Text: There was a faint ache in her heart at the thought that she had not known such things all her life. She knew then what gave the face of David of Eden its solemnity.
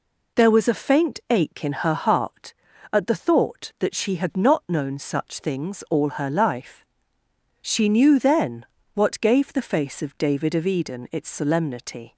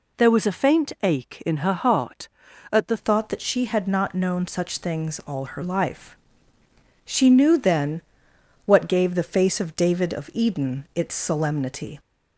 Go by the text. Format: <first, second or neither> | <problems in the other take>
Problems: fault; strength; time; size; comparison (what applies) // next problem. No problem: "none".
first | changes voice at "thought"; from 2.9 s on; 9.0 s long // pauses between "then" and "what"; noticeable; at 8.0 s; 0.66 s long; slight in the first